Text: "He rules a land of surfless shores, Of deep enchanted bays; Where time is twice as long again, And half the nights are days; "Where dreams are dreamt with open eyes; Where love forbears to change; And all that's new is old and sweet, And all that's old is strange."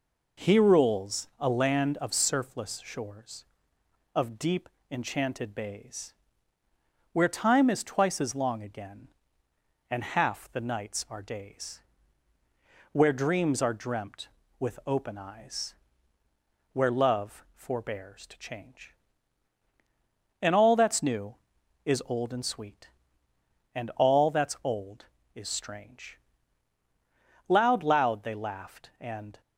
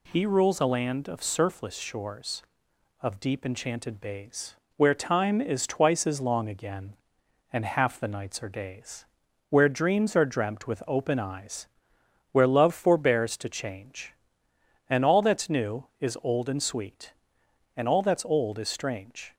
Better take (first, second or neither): second